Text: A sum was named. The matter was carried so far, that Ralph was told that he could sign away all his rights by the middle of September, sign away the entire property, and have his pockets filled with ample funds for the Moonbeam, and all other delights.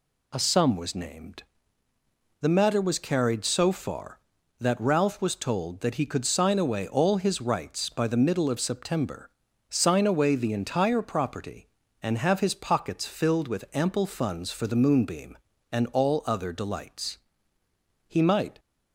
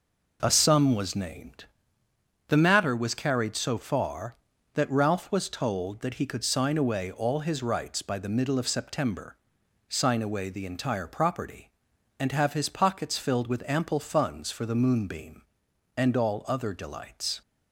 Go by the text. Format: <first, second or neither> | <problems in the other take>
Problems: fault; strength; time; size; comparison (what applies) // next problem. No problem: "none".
second | goes on to say "He might"; from 18.0 s on; 0.52 s long